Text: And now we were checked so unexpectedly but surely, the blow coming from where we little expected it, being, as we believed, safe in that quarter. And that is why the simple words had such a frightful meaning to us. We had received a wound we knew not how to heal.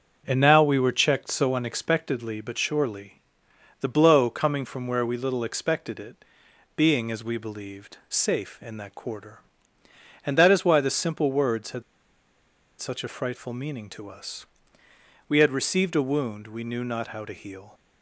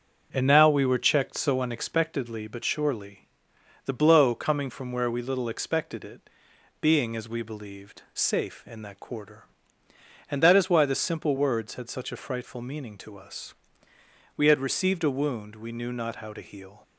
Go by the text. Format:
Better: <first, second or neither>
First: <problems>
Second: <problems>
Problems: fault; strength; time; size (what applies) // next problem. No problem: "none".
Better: second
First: starts louder than the rest; until 1.2 s; 7 dB // pauses between "had" and "such"; noticeable; at 11.8 s; 0.97 s long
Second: starts louder than the rest; until 1.3 s; 7 dB